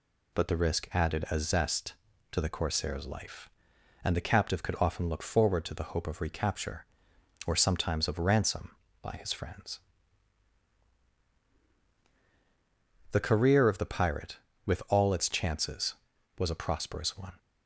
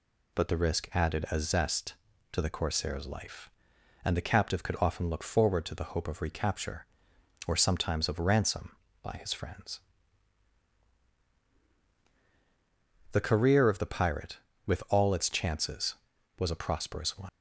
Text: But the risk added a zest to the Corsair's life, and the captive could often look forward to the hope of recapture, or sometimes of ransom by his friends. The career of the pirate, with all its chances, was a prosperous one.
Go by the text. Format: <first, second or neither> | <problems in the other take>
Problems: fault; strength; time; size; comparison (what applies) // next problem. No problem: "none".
first | leaves "one" unfinished; at 17.2 s; 90 ms